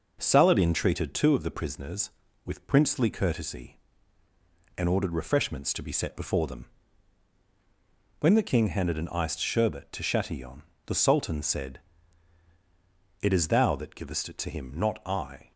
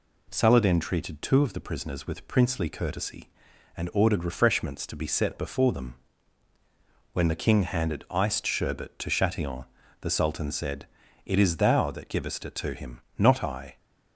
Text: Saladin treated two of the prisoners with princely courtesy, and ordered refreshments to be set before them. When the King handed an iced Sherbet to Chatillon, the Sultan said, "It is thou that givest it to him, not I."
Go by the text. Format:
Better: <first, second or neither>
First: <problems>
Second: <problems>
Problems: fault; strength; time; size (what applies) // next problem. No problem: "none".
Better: first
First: none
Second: skips "an"; at 8.0 s